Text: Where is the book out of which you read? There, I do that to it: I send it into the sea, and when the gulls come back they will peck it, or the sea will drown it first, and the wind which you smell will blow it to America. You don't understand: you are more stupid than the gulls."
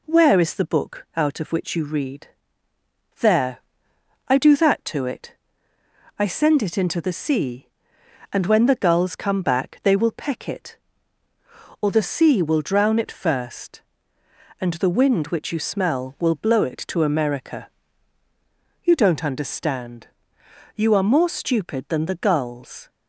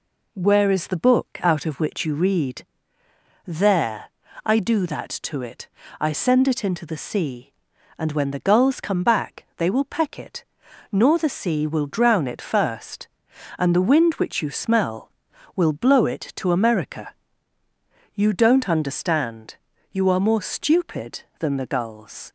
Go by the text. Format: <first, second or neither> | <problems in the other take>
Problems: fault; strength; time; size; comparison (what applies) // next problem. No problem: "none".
first | says "nor" for "or"; at 10.8 s